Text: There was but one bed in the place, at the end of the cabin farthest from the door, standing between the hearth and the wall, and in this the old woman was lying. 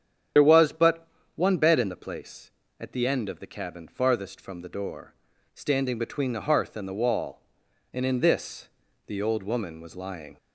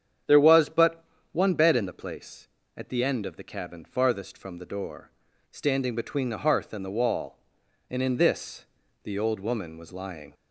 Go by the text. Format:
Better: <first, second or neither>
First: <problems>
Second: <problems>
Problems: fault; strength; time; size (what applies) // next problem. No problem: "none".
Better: second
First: loses the start of "There"; at 0.3 s; 50 ms // starts louder than the rest; strong; until 1.6 s; 8 dB // pauses between "but" and "one"; slight; at 1.0 s; 0.28 s long // pauses between "this" and "the"; at 8.6 s; 0.38 s long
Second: starts louder than the rest; strong; until 1.5 s; 8.5 dB // pauses between "but" and "one"; slight; at 1.0 s; 0.28 s long // pauses between "this" and "the"; at 8.6 s; 0.38 s long